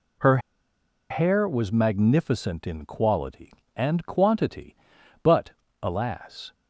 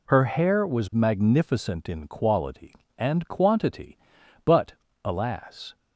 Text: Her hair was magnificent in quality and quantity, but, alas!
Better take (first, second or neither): second